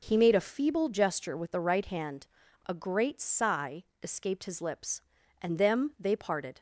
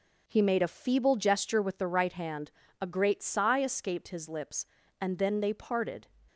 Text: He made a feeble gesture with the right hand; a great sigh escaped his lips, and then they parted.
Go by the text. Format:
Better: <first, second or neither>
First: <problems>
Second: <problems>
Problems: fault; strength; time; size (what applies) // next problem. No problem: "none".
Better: second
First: pauses between "sigh" and "escaped"; slight; at 3.8 s; 0.16 s long // says "them" for "then"; at 5.5 s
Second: none